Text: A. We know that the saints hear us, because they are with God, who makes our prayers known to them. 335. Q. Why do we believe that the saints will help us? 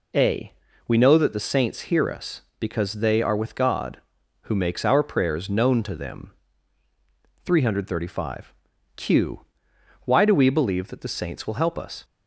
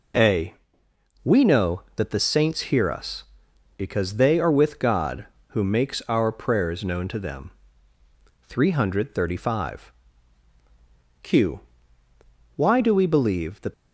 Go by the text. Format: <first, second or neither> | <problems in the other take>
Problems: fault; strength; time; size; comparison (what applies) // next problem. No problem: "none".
first | stops before "the saints will help us"; at 13.7 s